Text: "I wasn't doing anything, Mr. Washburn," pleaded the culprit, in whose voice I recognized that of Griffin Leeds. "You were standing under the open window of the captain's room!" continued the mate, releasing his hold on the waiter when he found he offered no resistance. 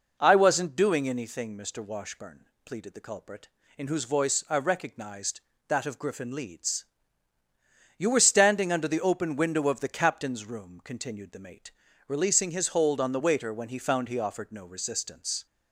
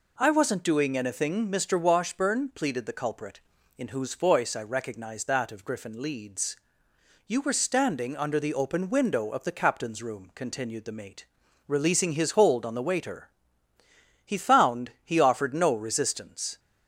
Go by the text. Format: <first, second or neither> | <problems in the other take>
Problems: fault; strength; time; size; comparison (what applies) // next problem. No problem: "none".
first | skips "when"; at 13.7 s